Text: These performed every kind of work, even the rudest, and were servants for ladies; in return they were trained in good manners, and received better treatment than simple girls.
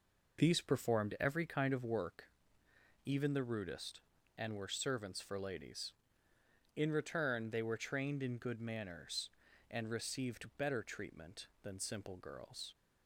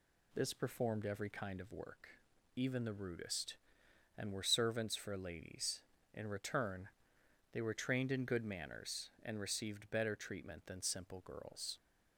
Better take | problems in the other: first | says "This" for "These"; at 0.3 s // pauses between "return" and "they"; noticeable; at 6.8 s; 0.64 s long

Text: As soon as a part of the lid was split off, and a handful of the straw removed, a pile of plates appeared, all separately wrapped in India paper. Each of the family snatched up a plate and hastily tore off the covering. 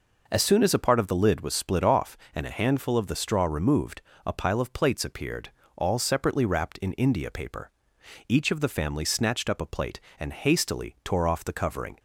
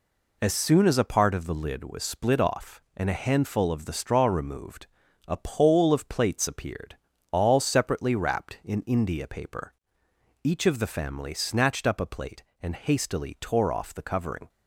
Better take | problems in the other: first | says "pole" for "pile"; at 5.3 s

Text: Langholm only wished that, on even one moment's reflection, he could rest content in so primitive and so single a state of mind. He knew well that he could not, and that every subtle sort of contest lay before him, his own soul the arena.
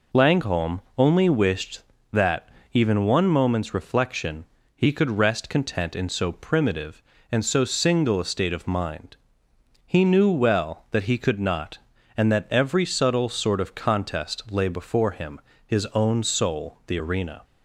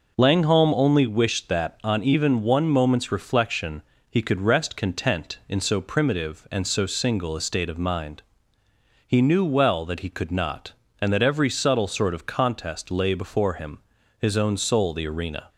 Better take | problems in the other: second | pauses between "Langholm" and "only"; slight; at 0.8 s; 0.16 s long // skips "on"; at 2.6 s

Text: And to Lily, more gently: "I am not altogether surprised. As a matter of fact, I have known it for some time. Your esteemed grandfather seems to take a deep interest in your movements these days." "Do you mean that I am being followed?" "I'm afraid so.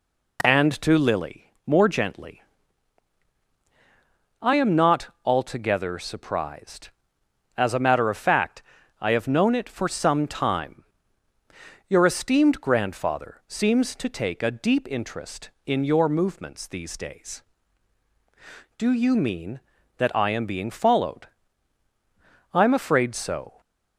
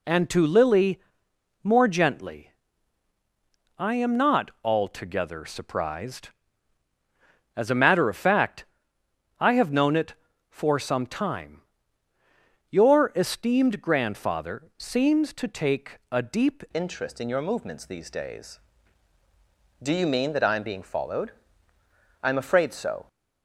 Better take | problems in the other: first | changes voice at "interest"; from 16.7 s on; 6.3 s long

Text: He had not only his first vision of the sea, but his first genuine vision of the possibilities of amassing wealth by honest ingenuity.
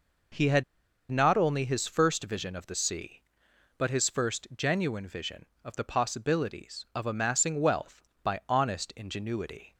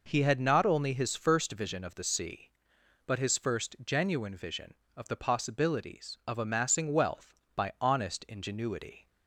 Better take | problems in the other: second | pauses between "had" and "not"; noticeable; at 0.6 s; 0.46 s long

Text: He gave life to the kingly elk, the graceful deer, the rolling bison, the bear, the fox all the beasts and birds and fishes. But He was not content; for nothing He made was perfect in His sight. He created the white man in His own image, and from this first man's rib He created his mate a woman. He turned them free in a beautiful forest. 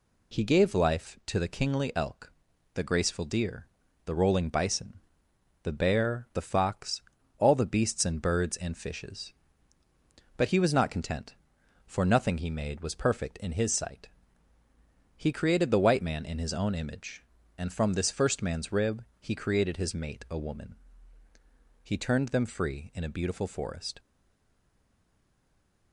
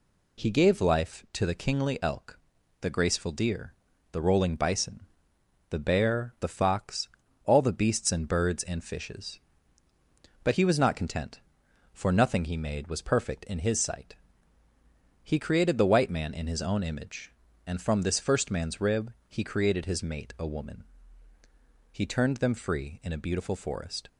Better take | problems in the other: second | pauses between "fox" and "all"; slight; at 7.0 s; 0.36 s long; slight in the second // pauses between "rib" and "He"; slight; at 19.0 s; 0.16 s long; slight in the second // stays silent after the last word; noticeable; from 23.9 s on; 2.0 s long

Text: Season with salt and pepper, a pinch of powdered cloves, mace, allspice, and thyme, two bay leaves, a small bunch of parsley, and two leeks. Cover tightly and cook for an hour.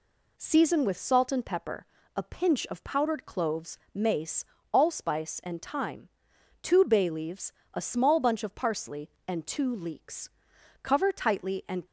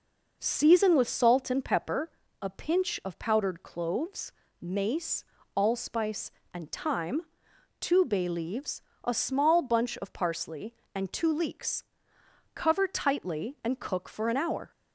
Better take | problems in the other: second | stops before "cook for an hour"; at 11.8 s

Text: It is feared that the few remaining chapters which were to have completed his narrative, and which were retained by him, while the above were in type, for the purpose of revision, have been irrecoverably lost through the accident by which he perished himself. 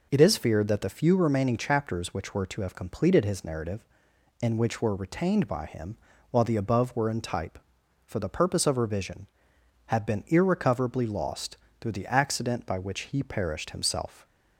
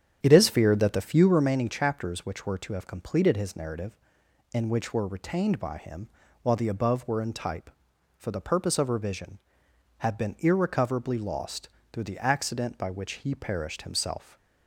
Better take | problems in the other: first | starts louder than the rest; strong; until 1.6 s; 8.5 dB // pauses between "lost" and "through"; slight; at 11.6 s; 0.24 s long; slight in the first

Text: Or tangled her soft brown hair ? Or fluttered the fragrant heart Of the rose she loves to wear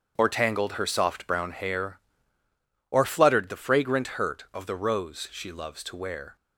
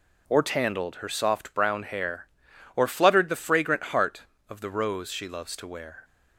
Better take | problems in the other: second | starts louder than the rest; strong; until 1.1 s; 7.5 dB // says "hurt" for "heart"; at 4.0 s

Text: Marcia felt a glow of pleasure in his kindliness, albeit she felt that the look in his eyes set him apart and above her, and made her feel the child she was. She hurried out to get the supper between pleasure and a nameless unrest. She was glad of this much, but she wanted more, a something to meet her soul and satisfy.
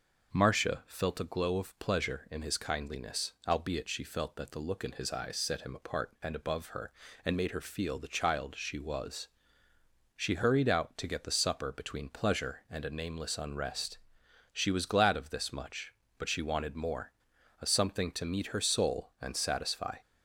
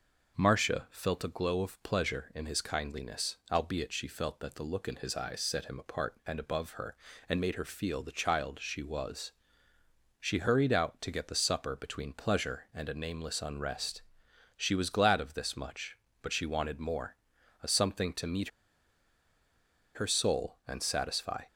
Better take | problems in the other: first | pauses between "meet" and "her"; strong; at 18.4 s; 1.4 s long

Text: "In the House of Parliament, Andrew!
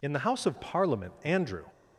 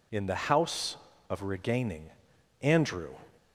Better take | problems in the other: first | says "Regaining" for "Parliament"; at 1.4 s

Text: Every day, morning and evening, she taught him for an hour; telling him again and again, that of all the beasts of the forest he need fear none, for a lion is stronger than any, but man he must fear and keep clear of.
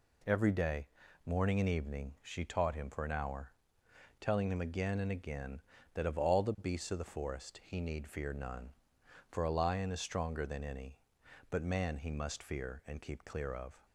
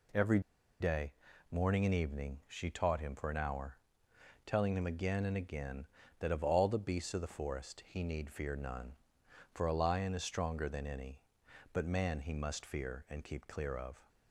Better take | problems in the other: first | pauses between "Every" and "day"; at 0.3 s; 0.40 s long

